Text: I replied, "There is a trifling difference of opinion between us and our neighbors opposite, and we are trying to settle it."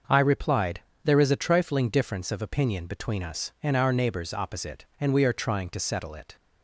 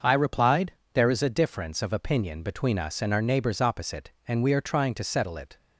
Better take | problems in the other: first | starts louder than the rest; until 1.2 s; 6.5 dB; noticeable in the first // skips "trifling"; at 1.2 s

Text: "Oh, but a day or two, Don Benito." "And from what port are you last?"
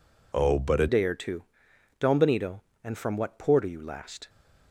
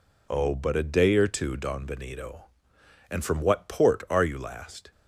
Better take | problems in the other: second | changes voice at "day"; from 0.8 s on; 3.4 s long

